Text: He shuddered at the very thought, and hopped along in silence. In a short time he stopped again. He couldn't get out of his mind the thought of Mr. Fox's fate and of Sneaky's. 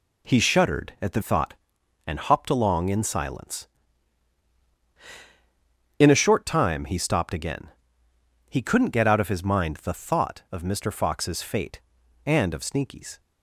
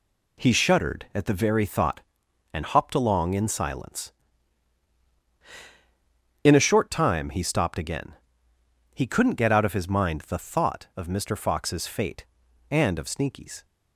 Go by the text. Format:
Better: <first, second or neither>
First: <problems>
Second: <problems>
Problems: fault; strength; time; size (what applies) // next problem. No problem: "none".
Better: second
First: skips "very"; at 1.2 s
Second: none